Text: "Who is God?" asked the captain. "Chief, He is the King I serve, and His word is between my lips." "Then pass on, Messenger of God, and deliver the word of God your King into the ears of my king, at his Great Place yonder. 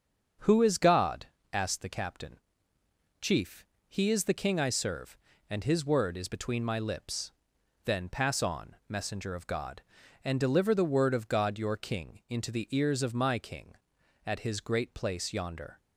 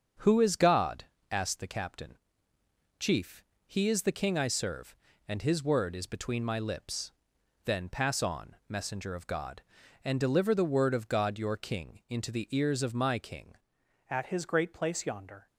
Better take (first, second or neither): first